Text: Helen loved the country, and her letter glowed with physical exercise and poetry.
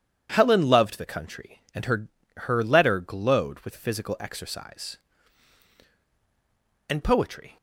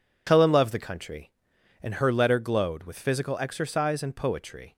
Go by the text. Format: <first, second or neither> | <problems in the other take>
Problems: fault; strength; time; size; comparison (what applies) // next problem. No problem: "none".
second | says "her" twice; at 2.4 s